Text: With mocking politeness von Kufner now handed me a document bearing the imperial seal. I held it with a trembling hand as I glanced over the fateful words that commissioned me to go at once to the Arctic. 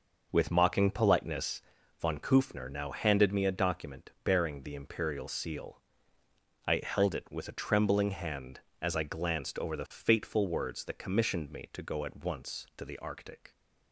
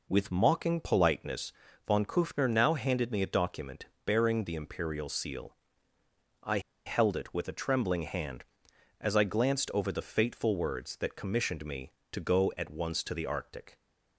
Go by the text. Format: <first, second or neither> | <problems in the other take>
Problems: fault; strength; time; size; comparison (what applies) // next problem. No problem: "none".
first | pauses between "politeness" and "von"; slight; at 1.5 s; 0.34 s long; slight in the first // pauses between "document" and "bearing"; slight; at 3.8 s; 0.20 s long // pauses between "I" and "held"; slight; at 6.5 s; 0.26 s long